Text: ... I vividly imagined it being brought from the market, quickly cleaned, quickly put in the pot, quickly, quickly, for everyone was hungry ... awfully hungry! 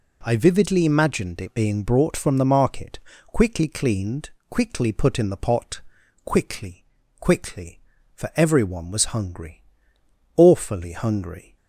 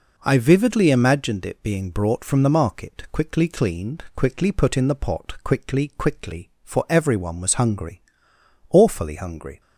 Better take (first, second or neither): first